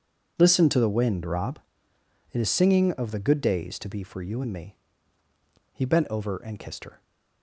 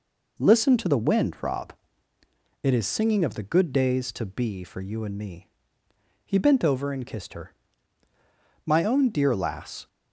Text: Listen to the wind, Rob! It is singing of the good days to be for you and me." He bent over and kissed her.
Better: first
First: none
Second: goes on to say "My own dear lass"; noticeable; from 8.6 s on; 1.2 s long

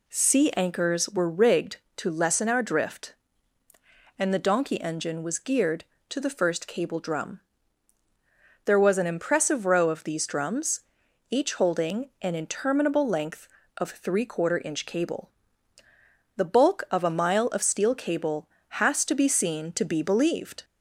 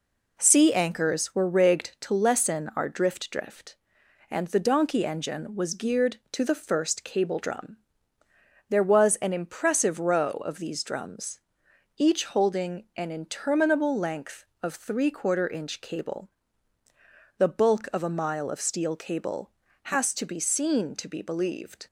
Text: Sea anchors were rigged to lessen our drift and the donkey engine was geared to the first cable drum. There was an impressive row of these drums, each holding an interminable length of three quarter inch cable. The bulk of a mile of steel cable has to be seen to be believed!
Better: first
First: none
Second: says "drift" twice; at 3.3 s

